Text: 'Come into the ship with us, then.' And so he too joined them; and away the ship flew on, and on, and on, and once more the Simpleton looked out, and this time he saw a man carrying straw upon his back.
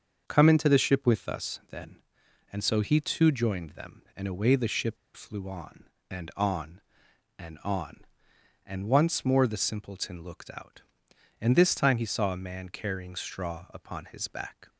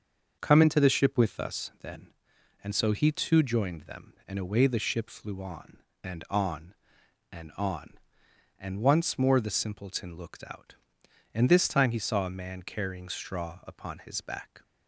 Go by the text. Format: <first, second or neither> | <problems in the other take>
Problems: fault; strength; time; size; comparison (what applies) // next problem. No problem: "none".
second | starts louder than the rest; until 1.2 s; 6.5 dB; also in the second // pauses between "ship" and "flew"; slight; at 4.9 s; 0.19 s long